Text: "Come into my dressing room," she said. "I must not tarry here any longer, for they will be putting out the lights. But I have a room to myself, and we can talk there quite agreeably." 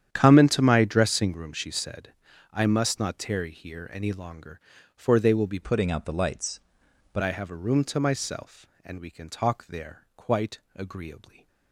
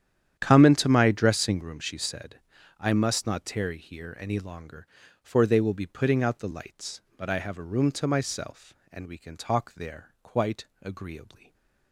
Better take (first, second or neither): second